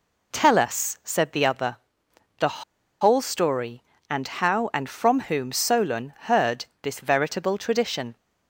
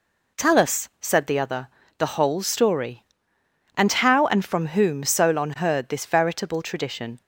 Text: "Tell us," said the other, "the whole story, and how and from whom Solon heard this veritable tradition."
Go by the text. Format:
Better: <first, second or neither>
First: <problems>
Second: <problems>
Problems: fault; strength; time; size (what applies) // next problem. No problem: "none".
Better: second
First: pauses between "the" and "whole"; at 2.6 s; 0.38 s long // pauses between "heard" and "this"; slight; at 6.6 s; 0.20 s long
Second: none